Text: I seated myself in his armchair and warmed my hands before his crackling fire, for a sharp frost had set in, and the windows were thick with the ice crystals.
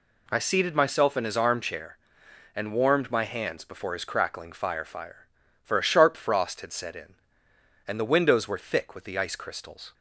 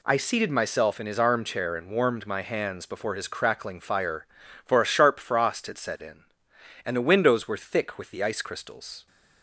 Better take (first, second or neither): second